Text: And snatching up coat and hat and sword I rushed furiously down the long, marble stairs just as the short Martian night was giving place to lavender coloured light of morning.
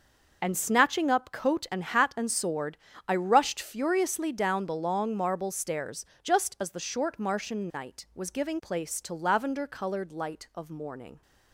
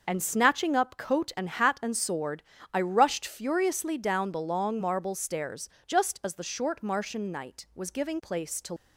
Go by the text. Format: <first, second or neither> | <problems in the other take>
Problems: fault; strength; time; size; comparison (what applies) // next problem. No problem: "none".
first | pauses between "sword" and "I"; slight; at 2.4 s; 0.28 s long; slight in the first // pauses between "stairs" and "just"; slight; at 5.6 s; 0.16 s long; slight in the first // stops before "lavender coloured light of morning"; at 8.7 s